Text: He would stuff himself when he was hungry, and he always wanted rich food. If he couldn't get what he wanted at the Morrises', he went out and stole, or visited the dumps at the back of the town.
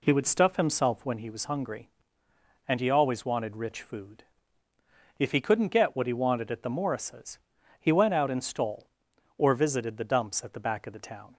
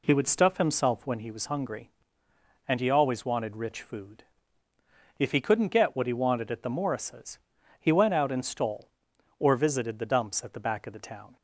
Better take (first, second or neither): neither